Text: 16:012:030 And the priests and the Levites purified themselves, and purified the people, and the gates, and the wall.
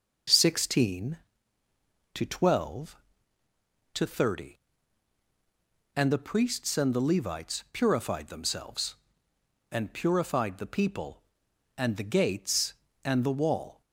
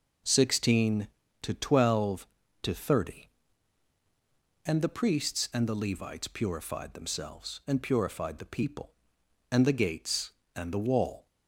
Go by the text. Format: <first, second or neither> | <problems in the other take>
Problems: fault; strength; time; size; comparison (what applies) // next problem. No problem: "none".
neither | none